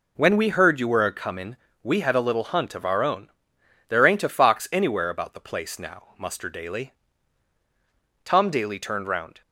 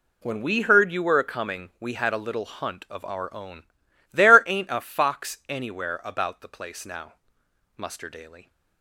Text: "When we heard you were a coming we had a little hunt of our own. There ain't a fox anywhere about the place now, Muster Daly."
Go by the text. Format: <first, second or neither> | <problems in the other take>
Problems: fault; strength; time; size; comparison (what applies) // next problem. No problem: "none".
second | pauses between "coming" and "we"; slight; at 1.5 s; 0.26 s long // goes on to say "Tom Daly turned round"; noticeable; from 8.2 s on; 1.1 s long